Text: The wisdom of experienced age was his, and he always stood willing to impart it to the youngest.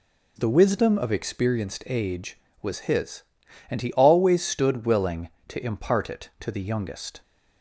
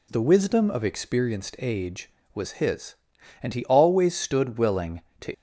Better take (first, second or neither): first